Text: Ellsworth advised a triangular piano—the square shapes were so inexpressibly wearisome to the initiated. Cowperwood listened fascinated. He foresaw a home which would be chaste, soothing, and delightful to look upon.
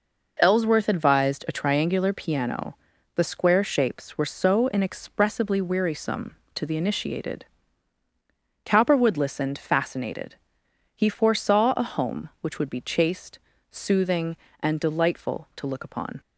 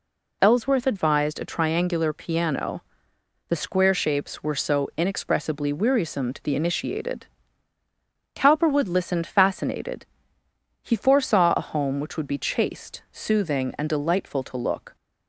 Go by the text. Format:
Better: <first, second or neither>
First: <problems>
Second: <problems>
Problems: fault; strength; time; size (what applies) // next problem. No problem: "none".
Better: first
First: none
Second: stops before "upon"; at 14.9 s